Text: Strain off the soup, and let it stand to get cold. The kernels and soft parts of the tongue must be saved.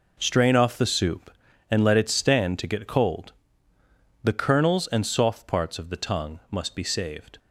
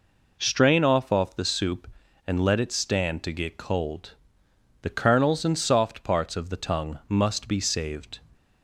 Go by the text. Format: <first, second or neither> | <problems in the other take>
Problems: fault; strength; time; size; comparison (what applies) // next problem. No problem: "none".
first | says "off" twice; at 1.1 s